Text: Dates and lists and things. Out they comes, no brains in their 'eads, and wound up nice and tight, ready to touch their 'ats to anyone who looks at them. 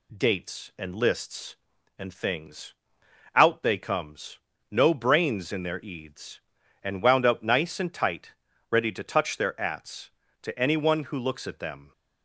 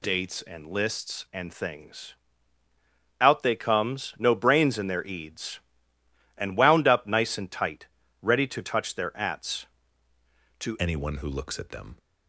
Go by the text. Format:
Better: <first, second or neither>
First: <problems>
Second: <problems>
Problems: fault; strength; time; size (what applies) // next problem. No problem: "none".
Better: first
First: none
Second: changes voice at "anyone"; from 10.8 s on; 1.1 s long